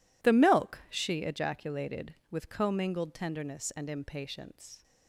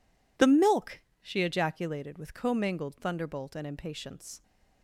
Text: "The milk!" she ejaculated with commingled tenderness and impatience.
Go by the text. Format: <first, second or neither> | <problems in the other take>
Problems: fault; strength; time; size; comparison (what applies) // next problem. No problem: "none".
first | says "thunderbolt" for "tenderness"; at 2.9 s